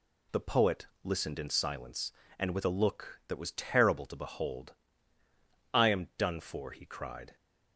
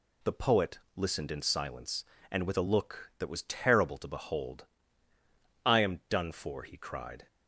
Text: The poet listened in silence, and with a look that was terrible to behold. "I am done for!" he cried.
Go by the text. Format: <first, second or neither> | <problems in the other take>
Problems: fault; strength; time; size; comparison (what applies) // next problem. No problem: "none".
neither | pauses between "poet" and "listened"; slight; the same in both